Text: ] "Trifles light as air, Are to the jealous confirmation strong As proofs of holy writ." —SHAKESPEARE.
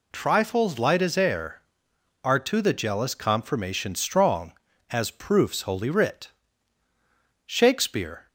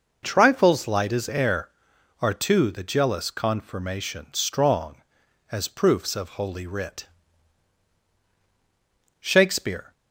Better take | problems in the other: second | skips "of"; at 5.6 s

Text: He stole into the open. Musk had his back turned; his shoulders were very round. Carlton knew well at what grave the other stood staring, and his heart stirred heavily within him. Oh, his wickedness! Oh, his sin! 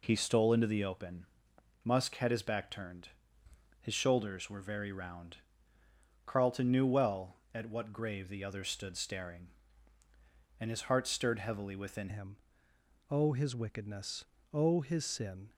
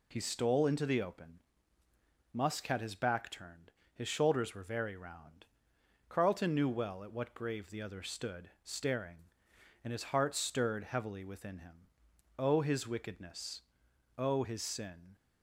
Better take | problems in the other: second | changes voice at "him"; from 12.0 s on; 3.5 s long

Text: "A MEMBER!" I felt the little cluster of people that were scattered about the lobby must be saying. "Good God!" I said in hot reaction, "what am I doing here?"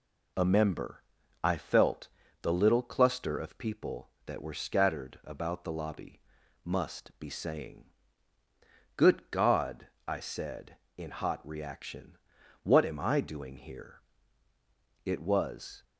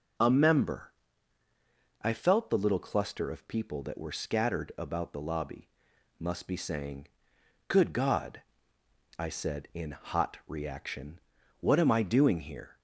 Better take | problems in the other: second | pauses between "felt" and "the"; slight; at 2.0 s; 0.34 s long // pauses between "lobby" and "must"; at 6.2 s; 0.42 s long; noticeable in the second // goes on to say "It was"; noticeable; from 15.0 s on; 0.78 s long

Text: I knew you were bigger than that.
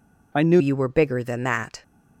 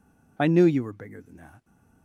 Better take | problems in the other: second | changes voice at "you"; from 0.5 s on; 1.3 s long

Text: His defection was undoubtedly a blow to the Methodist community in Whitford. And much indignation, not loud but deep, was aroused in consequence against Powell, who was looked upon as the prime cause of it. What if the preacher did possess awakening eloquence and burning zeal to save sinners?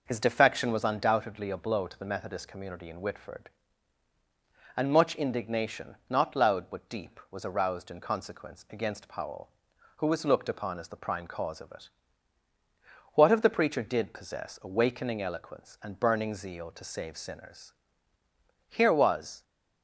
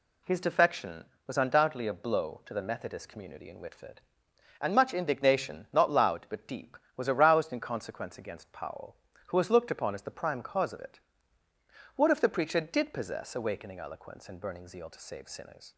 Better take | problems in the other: second | goes on to say "Here was"; noticeable; from 18.6 s on; 0.74 s long

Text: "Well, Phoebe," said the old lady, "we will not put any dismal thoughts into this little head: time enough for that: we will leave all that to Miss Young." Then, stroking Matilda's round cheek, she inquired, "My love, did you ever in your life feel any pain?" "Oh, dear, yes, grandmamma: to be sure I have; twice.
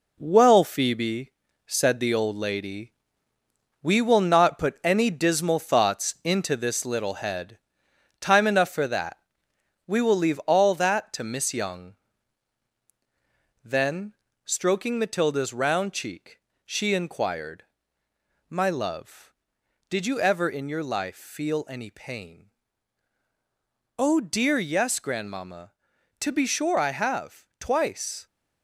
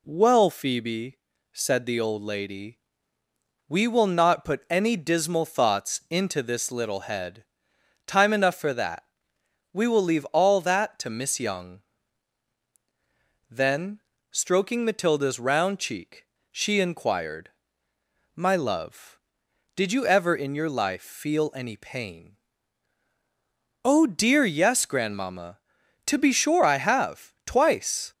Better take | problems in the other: second | gets quieter; noticeable; throughout; 6 dB

